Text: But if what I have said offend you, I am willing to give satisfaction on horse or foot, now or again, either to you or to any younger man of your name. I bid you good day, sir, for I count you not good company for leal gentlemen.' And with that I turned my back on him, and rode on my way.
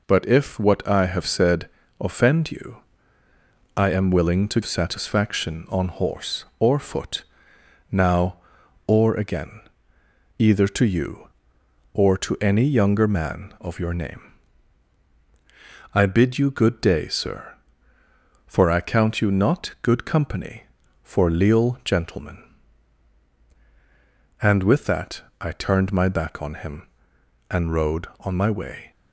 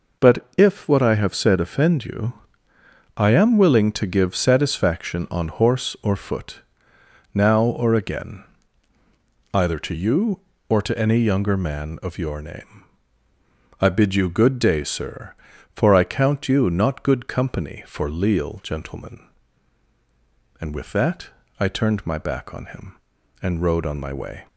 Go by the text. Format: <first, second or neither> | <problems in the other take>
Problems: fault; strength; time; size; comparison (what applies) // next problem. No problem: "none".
second | pauses between "said" and "offend"; slight; at 1.6 s; 0.30 s long // skips "give"; at 4.6 s // pauses between "that" and "I"; slight; at 25.2 s; 0.20 s long; slight in the second